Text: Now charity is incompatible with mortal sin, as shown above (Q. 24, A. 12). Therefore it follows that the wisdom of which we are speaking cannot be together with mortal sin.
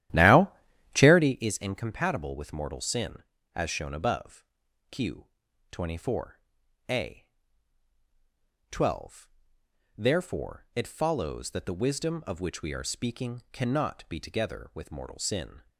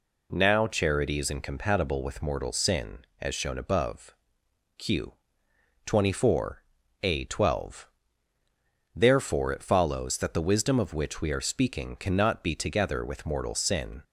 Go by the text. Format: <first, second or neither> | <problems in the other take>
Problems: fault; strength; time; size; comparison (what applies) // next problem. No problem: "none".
second | starts louder than the rest; strong; until 1.5 s; 12.5 dB // pauses between "Now" and "charity"; at 0.4 s; 0.44 s long